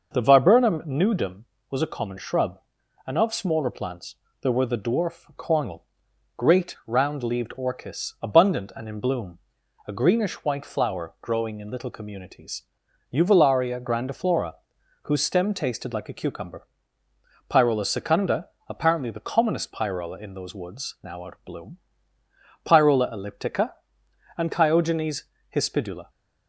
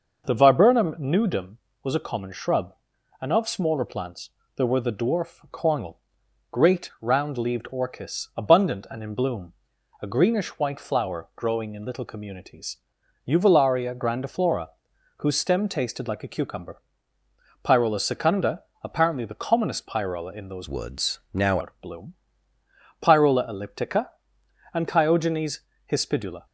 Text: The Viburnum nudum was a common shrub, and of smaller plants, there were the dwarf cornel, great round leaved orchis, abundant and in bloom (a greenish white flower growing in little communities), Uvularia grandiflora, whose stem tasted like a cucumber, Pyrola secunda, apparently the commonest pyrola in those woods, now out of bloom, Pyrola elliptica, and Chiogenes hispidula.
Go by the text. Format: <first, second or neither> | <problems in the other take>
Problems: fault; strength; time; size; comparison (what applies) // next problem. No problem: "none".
first | changes voice from "woods" to "now"; from 20.6 to 21.5 s; 0.9 s long // pauses between "Chiogenes" and "hispidula"; slight; at 25.6 s; 0.30 s long; slight in the first